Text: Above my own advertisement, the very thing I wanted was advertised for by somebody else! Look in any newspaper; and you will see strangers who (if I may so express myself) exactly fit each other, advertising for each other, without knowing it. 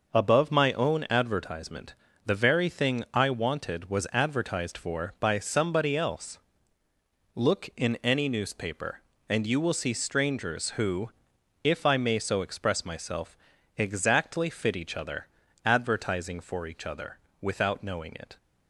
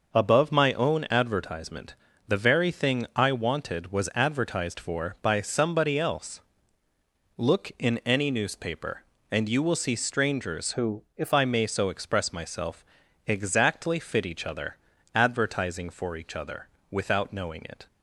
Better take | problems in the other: first | starts louder than the rest; noticeable; until 1.2 s; 6 dB; noticeable in the first // changes voice from "who" to "if"; from 10.7 to 11.3 s; 0.6 s long

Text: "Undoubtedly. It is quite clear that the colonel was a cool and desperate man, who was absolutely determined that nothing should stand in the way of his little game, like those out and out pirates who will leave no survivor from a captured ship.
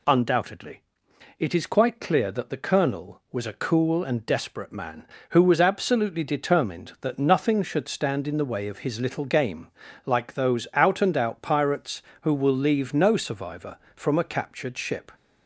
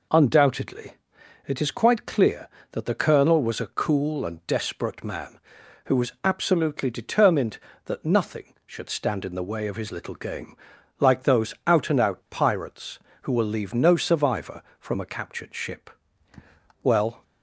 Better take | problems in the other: first | goes on to say "Well"; slight; from 16.8 s on; 0.40 s long

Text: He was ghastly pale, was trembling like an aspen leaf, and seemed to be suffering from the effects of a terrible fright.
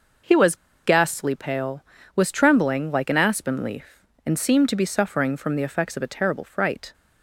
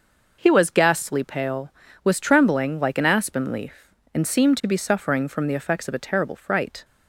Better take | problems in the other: second | pauses between "was" and "ghastly"; slight; at 0.5 s; 0.28 s long

